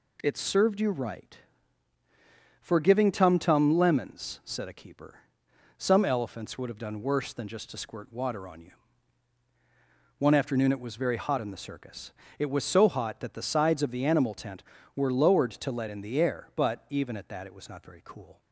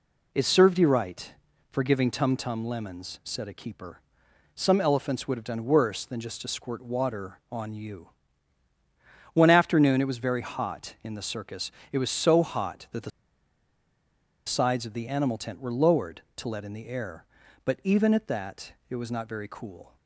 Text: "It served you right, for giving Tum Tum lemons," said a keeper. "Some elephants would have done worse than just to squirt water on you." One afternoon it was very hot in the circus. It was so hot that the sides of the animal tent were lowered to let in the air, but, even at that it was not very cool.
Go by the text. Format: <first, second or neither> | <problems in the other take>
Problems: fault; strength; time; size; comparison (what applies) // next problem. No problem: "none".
first | pauses between "the" and "sides"; strong; at 13.0 s; 1.3 s long